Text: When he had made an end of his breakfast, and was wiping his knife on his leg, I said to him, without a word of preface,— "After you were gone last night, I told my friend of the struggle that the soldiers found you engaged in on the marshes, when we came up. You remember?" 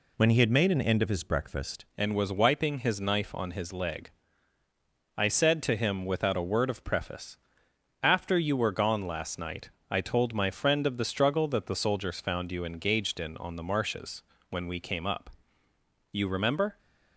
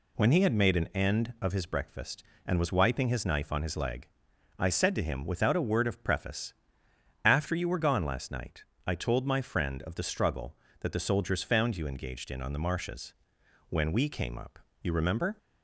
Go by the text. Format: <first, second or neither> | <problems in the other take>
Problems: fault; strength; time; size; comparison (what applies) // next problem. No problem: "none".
second | changes voice at "and"; from 1.9 s on; 14.8 s long